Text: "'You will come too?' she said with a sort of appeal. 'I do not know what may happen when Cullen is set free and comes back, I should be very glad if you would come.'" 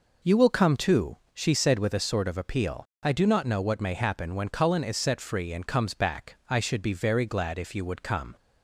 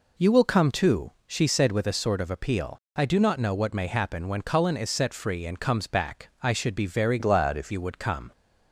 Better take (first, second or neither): first